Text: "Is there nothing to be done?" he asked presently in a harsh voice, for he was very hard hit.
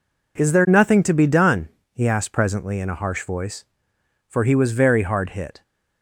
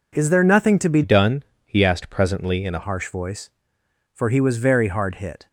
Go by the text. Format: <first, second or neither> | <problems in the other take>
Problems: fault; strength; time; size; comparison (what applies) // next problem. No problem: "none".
first | changes voice from "done" to "a"; from 1.0 to 2.8 s; 1.8 s long